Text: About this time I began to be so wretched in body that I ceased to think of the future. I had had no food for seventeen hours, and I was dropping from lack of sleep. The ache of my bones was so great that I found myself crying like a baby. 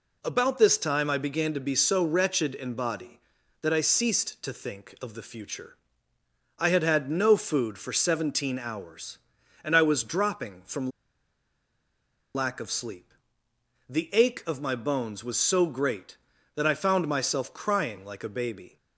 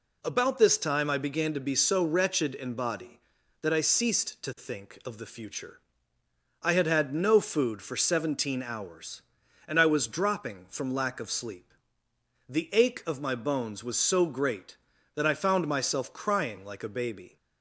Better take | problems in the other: second | pauses between "from" and "lack"; strong; at 10.9 s; 1.4 s long

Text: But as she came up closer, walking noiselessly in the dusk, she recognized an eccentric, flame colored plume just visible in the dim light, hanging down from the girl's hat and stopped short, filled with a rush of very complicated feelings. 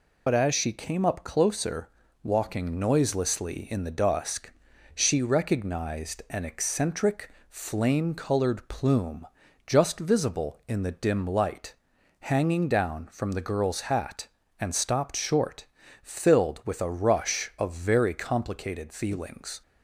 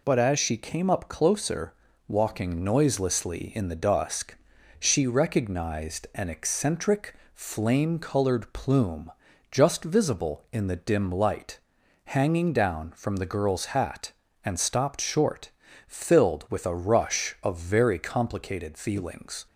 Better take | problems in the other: second | loses the start of "But"; at 0.2 s; 70 ms // pauses between "plume" and "just"; at 9.2 s; 0.40 s long; also in the second

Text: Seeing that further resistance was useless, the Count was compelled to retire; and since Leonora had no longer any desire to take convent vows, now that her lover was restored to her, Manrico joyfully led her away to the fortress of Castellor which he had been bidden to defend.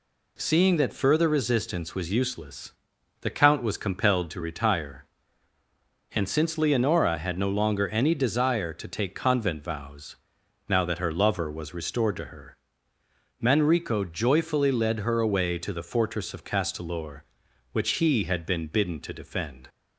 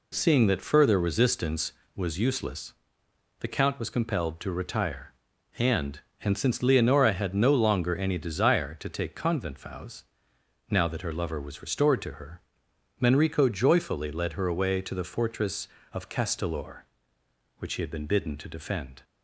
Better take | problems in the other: first | says "and" twice; at 6.2 s

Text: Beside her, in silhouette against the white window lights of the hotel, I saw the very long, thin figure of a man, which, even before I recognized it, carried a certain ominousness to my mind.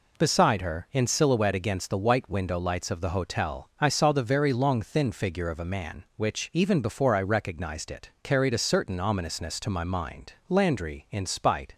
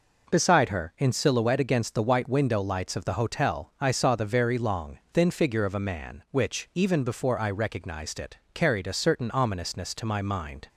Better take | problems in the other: second | goes on to say "Landry in spite"; noticeable; from 10.4 s on; 1.2 s long

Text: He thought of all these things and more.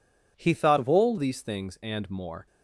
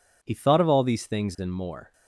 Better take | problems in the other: second | changes voice from "of" to "all"; from 0.7 to 1.1 s; 0.4 s long

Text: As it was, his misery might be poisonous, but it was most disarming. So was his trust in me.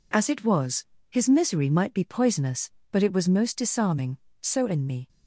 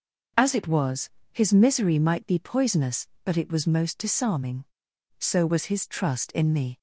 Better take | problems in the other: second | skips "was his trust"; at 4.6 s

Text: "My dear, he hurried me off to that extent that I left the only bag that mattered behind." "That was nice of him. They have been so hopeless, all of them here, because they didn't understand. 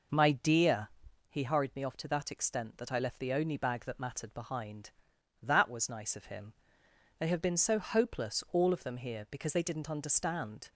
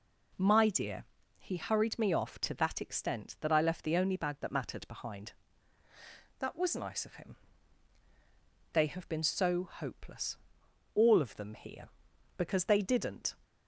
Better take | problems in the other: first | stops before "understand"; at 13.4 s

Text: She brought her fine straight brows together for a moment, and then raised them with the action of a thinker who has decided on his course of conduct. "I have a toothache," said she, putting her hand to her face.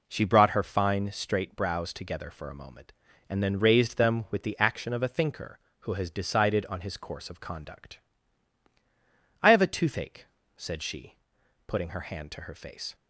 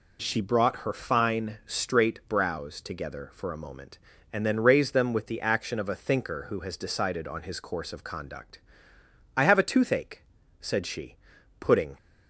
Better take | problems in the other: first | stops before "her hand to her face"; at 11.9 s

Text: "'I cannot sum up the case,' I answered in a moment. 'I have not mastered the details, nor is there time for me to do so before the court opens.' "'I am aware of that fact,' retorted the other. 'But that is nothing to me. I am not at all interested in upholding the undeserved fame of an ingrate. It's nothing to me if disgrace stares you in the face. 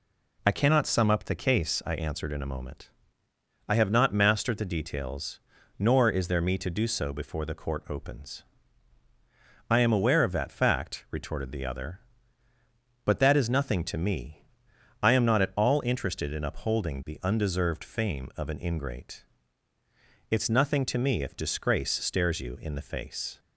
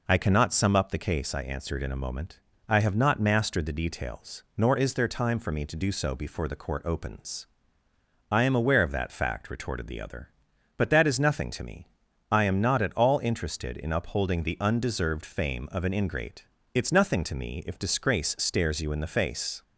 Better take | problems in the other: second | skips "time for"; at 6.4 s

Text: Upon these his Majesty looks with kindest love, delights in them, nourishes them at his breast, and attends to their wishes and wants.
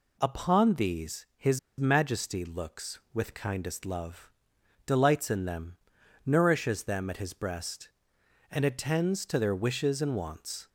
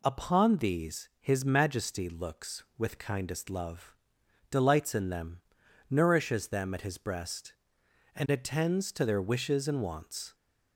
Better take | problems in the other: second | pauses between "his" and "Majesty"; slight; at 1.5 s; 0.20 s long

